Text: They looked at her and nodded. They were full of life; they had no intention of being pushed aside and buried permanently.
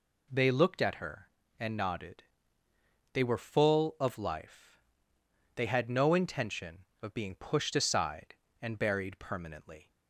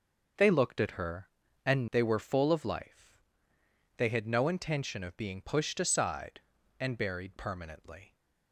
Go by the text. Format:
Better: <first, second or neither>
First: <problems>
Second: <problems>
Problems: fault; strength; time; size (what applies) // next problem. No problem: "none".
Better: first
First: none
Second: starts louder than the rest; until 1.7 s; 6.5 dB // skips "nodded"; at 1.8 s